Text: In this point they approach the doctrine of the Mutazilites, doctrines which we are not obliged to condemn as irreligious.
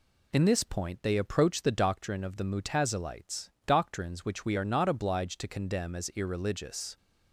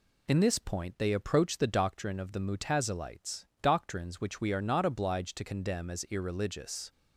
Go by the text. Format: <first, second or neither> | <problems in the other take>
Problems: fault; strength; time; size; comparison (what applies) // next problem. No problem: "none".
neither | none